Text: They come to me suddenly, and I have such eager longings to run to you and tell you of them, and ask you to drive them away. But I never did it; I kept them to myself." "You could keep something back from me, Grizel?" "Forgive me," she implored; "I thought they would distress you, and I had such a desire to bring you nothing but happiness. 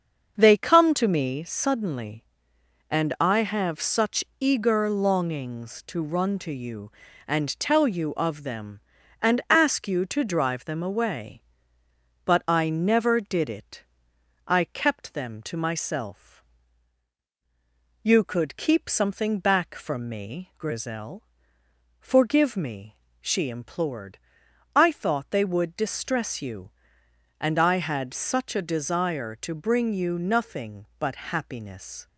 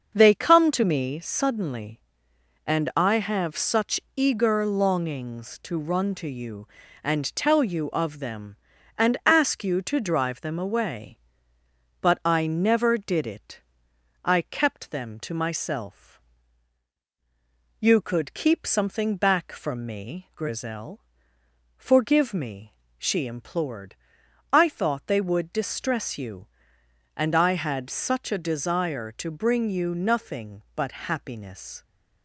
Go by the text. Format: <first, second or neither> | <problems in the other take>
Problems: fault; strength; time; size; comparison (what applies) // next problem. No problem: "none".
neither | starts louder than the rest; the same in both // pauses between "such" and "eager"; slight; the same in both